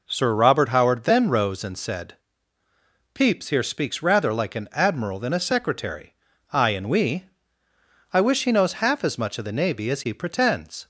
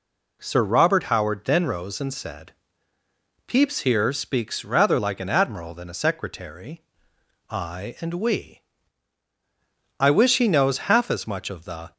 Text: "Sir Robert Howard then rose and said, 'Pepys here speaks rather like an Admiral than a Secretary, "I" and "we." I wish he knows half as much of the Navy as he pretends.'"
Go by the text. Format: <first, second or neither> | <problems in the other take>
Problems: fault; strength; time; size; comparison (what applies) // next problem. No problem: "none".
first | stops before "Navy as he pretends"; at 11.9 s